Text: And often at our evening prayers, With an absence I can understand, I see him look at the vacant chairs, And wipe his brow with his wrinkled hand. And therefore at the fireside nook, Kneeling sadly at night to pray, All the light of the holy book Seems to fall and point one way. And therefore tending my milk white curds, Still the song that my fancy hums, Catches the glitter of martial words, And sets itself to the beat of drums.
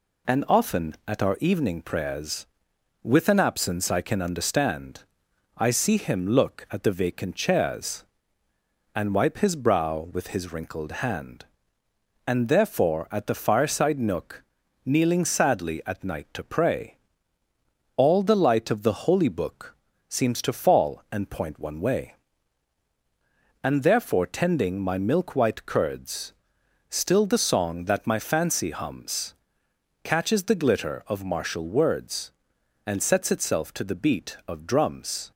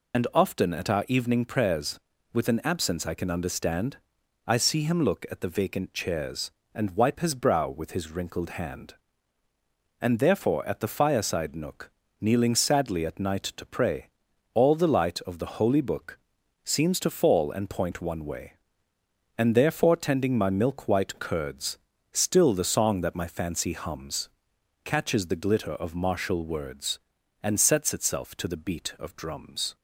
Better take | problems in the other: first | loses the start of "And"; at 0.1 s; 50 ms // pauses between "book" and "Seems"; noticeable; at 16.1 s; 0.46 s long; slight in the first

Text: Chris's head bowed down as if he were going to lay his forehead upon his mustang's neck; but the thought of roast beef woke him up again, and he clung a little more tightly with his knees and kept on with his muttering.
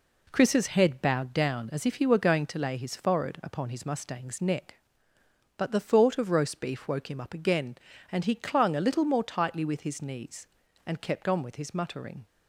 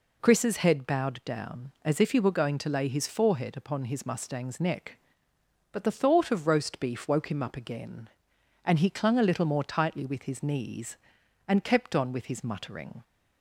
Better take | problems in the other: neither | none

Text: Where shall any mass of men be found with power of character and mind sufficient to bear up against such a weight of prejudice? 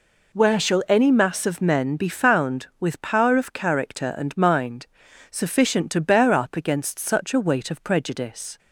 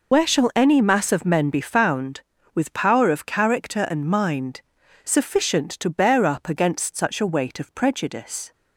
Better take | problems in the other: first | loses the start of "Where"; at 0.1 s; 50 ms // pauses between "mind" and "sufficient"; at 4.6 s; 0.42 s long; also in the first

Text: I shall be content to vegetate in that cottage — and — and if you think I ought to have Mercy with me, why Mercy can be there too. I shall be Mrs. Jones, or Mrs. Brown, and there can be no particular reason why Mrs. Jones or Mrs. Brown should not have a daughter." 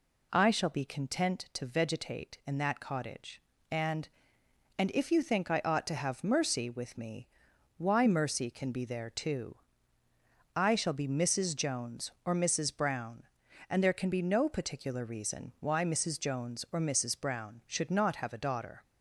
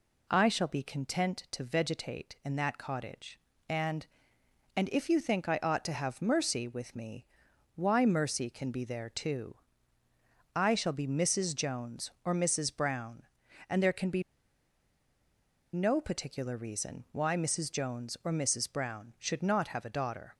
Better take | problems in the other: first | pauses between "be" and "no"; strong; at 14.2 s; 1.5 s long

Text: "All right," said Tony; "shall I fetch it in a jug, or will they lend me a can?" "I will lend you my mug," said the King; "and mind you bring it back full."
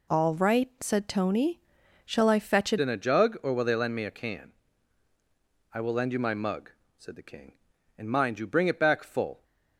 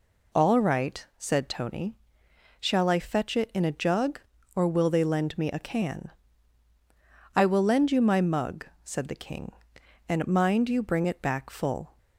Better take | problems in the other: second | changes voice at "in"; from 2.7 s on; 6.7 s long

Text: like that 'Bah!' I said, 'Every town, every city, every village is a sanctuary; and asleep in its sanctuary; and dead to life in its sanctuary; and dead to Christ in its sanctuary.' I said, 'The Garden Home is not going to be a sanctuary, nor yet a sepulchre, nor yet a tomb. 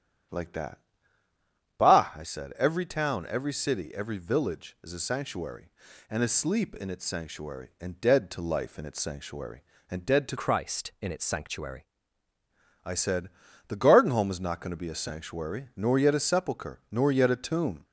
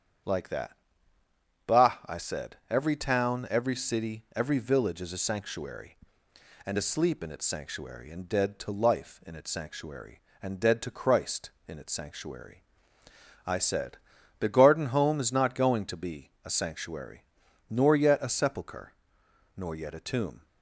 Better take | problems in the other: second | starts louder than the rest; strong; until 2.3 s; 9.5 dB; strong in the second // pauses between "that" and "Bah"; at 0.7 s; 1.0 s long; noticeable in the second // changes voice from "Christ" to "sanctuary"; from 10.3 to 11.8 s; 1.5 s long

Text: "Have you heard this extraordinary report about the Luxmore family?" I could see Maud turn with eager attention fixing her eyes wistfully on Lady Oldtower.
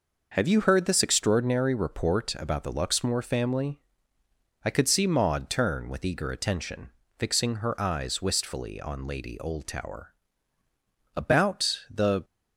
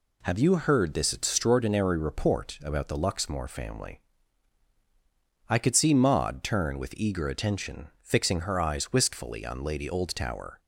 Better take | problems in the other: second | pauses between "attention" and "fixing"; slight; at 6.8 s; 0.30 s long; slight in the second // goes on to say "About the"; noticeable; from 11.1 s on; 1.1 s long

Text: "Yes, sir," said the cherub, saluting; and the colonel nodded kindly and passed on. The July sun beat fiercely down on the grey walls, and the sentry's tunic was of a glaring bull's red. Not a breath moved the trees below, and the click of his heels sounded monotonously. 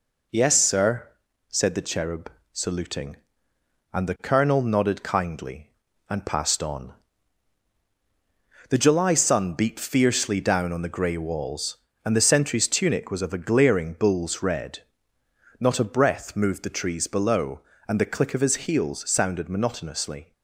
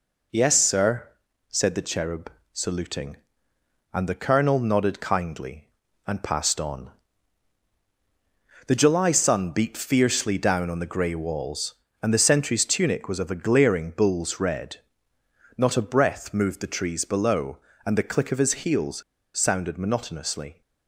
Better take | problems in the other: first | pauses between "heels" and "sounded"; at 19.0 s; 0.36 s long

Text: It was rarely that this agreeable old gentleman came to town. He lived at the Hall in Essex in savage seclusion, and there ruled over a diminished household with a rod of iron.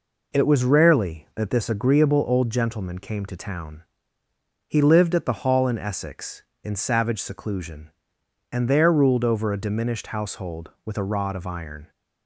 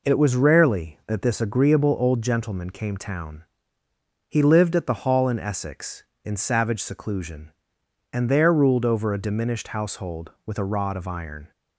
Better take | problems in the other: first | skips "to"; at 2.9 s

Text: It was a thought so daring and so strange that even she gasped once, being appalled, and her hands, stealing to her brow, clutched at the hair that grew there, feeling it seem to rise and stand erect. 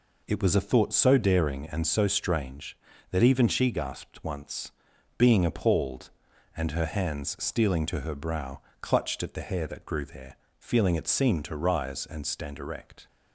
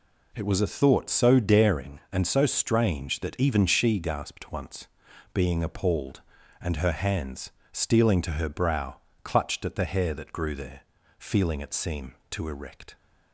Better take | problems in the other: first | skips "rise and stand"; at 12.4 s

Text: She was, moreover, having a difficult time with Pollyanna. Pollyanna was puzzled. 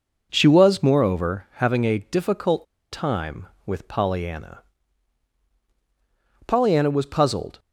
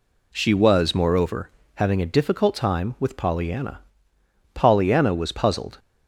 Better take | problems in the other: second | pauses between "difficult" and "time"; slight; at 2.6 s; 0.27 s long

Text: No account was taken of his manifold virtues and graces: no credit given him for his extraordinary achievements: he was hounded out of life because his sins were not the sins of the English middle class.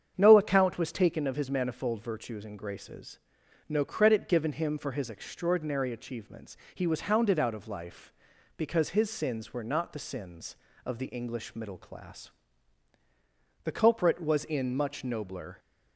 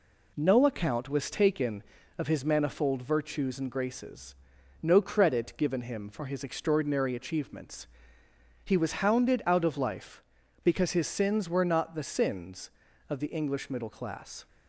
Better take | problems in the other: second | starts louder than the rest; strong; until 1.1 s; 7.5 dB // goes on to say "The culprit was in much nobler"; strong; from 13.6 s on; 1.9 s long

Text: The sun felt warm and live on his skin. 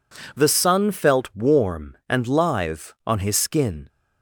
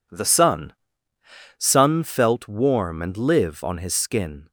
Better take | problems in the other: first | says "sun" twice; at 1.5 s

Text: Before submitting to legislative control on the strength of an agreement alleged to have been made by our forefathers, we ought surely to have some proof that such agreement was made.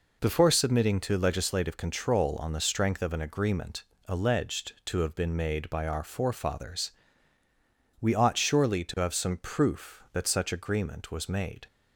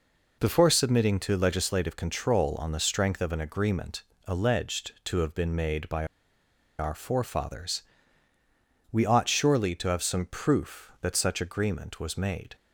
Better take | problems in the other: first | pauses between "agreement" and "alleged"; slight; at 4.0 s; 0.22 s long; slight in the first // pauses between "by" and "our"; noticeable; at 6.0 s; 0.72 s long

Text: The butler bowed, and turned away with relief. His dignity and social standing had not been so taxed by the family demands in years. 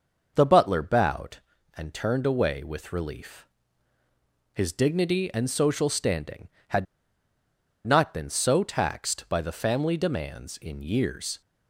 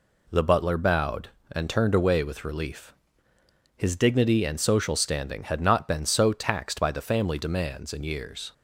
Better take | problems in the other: second | pauses between "had" and "not"; at 6.8 s; 1.0 s long

